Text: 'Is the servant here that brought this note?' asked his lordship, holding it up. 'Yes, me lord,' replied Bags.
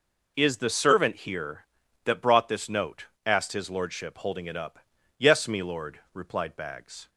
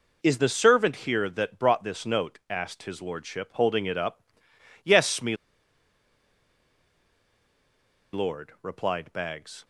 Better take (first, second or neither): first